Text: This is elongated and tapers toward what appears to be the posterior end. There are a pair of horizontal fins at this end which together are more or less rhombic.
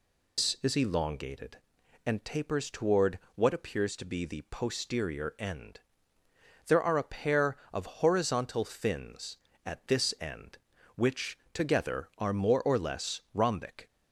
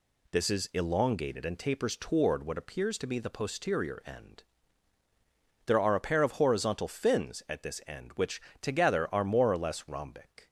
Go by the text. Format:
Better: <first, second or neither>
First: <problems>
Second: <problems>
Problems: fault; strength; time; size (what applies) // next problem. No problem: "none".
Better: second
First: loses the start of "This"; at 0.3 s; 135 ms // pauses between "toward" and "what"; slight; at 3.1 s; 0.16 s long // pauses between "of" and "horizontal"; slight; at 7.8 s; 0.16 s long // pauses between "which" and "together"; slight; at 11.3 s; 0.16 s long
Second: pauses between "which" and "together"; slight; at 8.4 s; 0.20 s long